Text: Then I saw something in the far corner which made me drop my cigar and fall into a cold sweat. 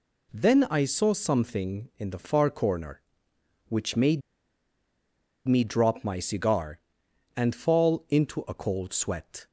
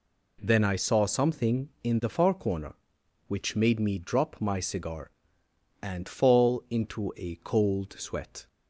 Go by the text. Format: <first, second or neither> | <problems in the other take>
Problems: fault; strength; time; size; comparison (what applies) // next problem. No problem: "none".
second | pauses between "made" and "me"; strong; at 4.2 s; 1.2 s long